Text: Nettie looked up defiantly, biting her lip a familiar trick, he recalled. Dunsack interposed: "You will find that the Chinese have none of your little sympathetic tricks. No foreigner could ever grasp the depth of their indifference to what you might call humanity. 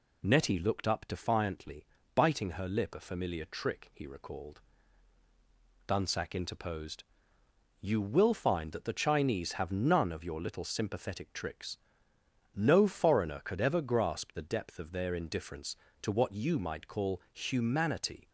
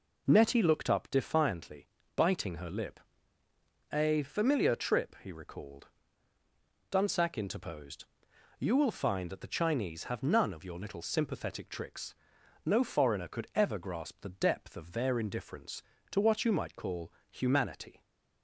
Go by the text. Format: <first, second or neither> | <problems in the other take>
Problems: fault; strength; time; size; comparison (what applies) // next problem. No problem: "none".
first | pauses between "lip" and "a"; noticeable; at 2.9 s; 0.94 s long // says "trip" for "trick"; at 4.7 s // pauses between "call" and "humanity"; slight; at 17.1 s; 0.16 s long